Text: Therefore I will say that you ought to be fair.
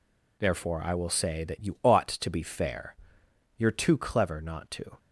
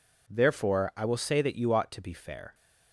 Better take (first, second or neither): second